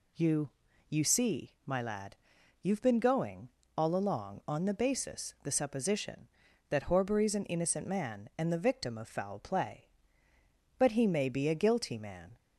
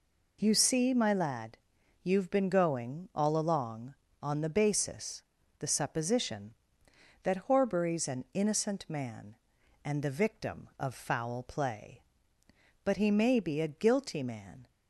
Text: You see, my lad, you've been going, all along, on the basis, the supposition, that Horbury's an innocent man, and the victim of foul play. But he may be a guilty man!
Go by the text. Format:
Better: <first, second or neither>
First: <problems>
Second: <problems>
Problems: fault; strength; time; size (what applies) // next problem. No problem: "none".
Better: second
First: says "You" twice; at 0.8 s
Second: none